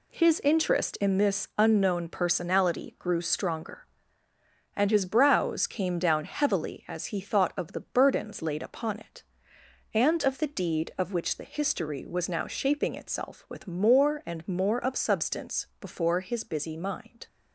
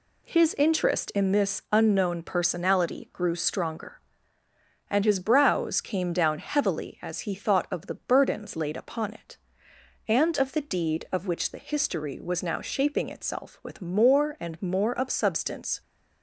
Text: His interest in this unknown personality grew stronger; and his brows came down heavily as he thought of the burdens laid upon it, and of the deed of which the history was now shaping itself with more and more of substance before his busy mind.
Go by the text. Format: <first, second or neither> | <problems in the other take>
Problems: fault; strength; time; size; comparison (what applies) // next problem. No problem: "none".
first | stops before "before his busy mind"; at 15.8 s